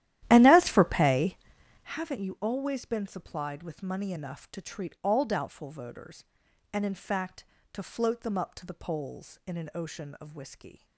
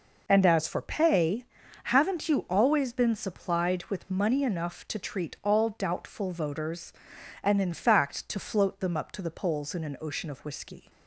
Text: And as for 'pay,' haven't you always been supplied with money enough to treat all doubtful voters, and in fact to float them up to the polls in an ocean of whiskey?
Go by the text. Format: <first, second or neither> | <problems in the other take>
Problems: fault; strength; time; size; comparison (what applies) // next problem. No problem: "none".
second | starts louder than the rest; strong; until 2.0 s; 13 dB